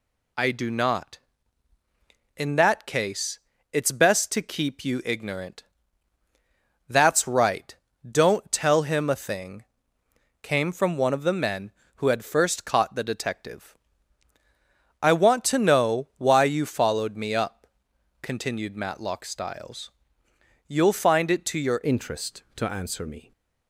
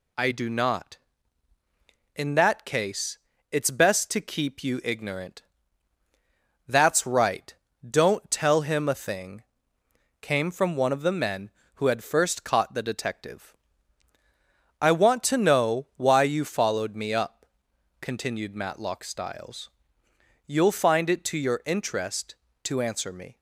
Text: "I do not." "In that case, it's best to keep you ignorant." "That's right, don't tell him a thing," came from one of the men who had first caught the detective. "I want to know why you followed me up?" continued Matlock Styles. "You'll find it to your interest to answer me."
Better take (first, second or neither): second